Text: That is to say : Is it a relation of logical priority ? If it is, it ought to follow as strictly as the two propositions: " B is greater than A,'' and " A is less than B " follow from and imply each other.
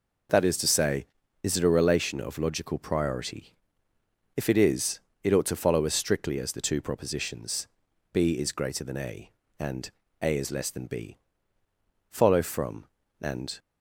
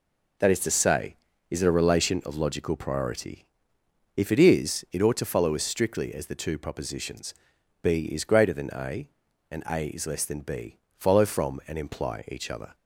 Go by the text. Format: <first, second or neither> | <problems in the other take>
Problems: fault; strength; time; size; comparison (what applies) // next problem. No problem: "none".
second | stops before "imply each other"; at 13.5 s